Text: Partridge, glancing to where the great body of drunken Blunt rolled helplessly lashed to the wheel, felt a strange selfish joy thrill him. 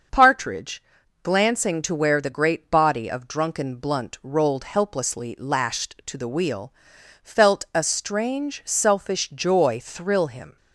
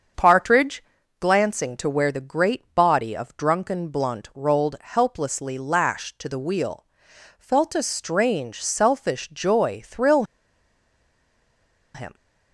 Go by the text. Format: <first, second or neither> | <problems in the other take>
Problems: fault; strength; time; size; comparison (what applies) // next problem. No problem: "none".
first | starts louder than the rest; strong; until 1.5 s; 7 dB; also in the first // pauses between "thrill" and "him"; strong; at 10.2 s; 1.7 s long